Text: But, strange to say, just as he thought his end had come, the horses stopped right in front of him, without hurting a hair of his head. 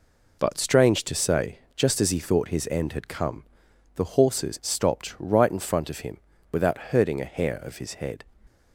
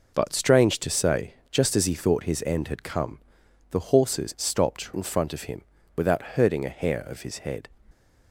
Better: first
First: none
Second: skips "right"; at 4.9 s

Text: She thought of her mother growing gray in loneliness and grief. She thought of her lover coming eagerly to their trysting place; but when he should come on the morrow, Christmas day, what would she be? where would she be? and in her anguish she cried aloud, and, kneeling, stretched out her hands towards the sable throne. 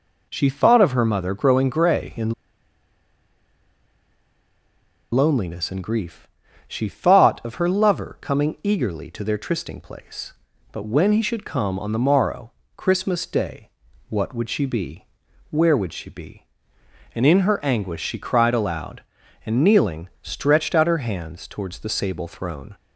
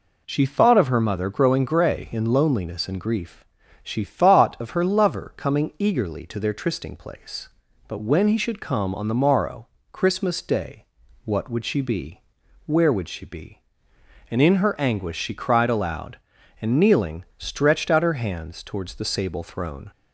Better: second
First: pauses between "in" and "loneliness"; strong; at 2.3 s; 2.8 s long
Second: none

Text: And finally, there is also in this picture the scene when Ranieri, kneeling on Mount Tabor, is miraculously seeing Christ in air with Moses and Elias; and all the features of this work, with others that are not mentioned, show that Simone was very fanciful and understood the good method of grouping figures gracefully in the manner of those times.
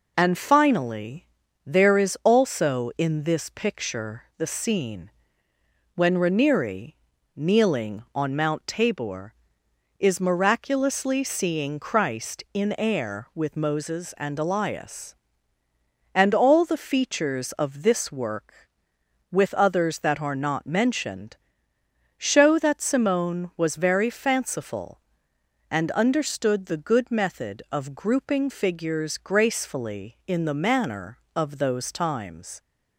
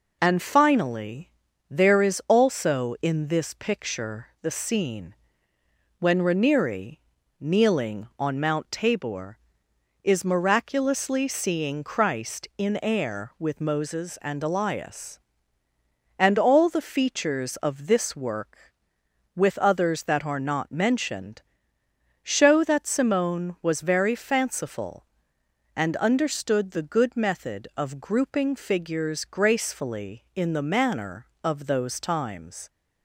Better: neither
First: pauses between "scene" and "when"; noticeable; at 5.1 s; 0.84 s long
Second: pauses between "scene" and "when"; noticeable; at 5.1 s; 0.84 s long

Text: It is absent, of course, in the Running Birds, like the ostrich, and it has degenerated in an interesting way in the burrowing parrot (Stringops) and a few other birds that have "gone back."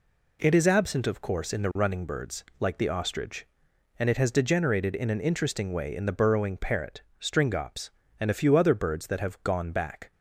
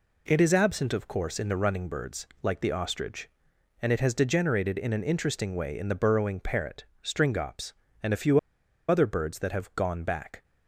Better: first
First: none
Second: pauses between "few" and "other"; noticeable; at 8.3 s; 0.50 s long

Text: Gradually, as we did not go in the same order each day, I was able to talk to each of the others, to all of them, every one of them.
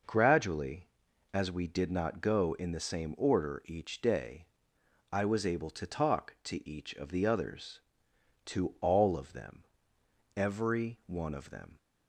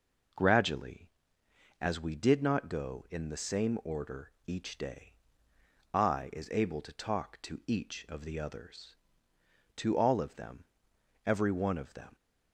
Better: first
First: none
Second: pauses between "order" and "each"; slight; at 4.3 s; 0.16 s long // says "is" for "was"; at 6.3 s

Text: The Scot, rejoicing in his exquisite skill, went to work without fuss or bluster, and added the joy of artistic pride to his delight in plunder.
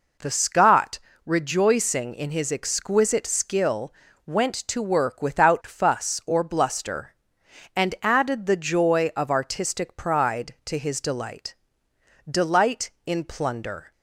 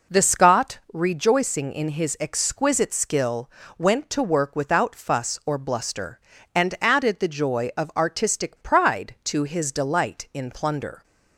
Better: second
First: says "delight" twice; at 12.2 s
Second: none

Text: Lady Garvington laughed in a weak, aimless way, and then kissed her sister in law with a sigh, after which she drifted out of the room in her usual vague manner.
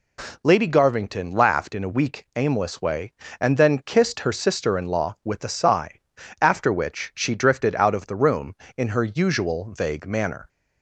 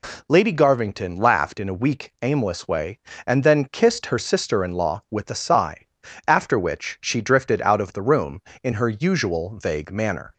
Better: neither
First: none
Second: none

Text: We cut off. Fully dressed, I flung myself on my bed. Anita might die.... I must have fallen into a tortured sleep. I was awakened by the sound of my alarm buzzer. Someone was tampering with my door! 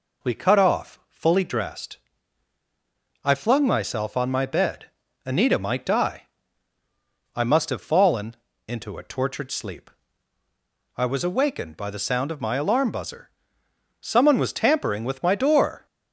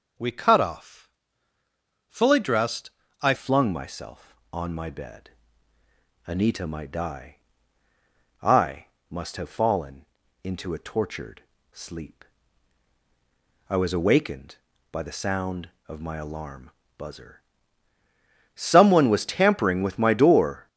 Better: first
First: pauses between "fallen" and "into"; slight; at 8.3 s; 0.32 s long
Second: changes voice at "flung"; from 3.3 s on; 17.3 s long // pauses between "I" and "must"; slight; at 8.8 s; 0.24 s long // pauses between "fallen" and "into"; at 10.0 s; 0.38 s long // pauses between "tortured" and "sleep"; slight; at 11.4 s; 0.32 s long // pauses between "alarm" and "buzzer"; slight; at 16.6 s; 0.30 s long

